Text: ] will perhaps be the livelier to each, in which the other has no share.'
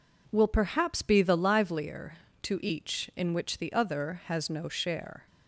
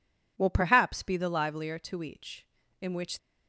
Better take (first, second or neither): first